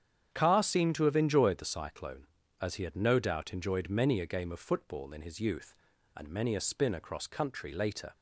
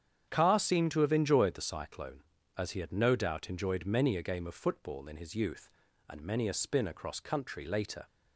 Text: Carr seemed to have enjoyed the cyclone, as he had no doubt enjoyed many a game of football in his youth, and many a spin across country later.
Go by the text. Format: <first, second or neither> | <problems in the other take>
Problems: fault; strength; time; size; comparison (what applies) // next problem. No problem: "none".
neither | starts louder than the rest; strong; the same in both